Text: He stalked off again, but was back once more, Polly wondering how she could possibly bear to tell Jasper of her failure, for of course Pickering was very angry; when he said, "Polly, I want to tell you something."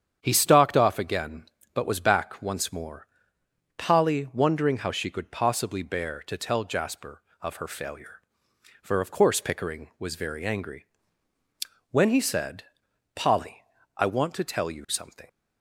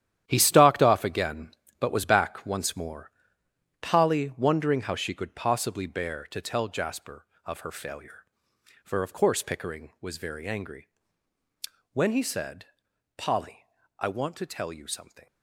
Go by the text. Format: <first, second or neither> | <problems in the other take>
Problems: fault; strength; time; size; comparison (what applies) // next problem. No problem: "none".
first | gets quieter; strong; throughout; 11 dB // starts louder than the rest; strong; until 1.2 s; 11 dB; strong in the first